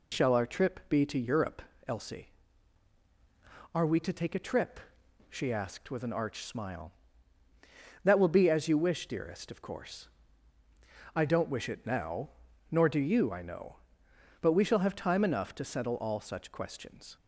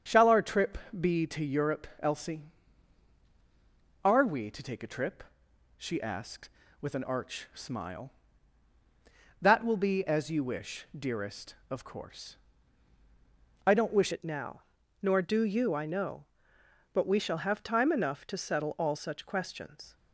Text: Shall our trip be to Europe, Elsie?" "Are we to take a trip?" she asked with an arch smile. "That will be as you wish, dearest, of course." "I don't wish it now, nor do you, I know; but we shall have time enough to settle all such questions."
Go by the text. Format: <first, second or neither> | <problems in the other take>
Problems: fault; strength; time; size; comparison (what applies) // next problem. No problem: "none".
first | starts louder than the rest; strong; until 1.3 s; 7 dB // pauses between "trip" and "be"; slight; at 0.7 s; 0.24 s long // changes voice at "it"; from 14.1 s on; 5.8 s long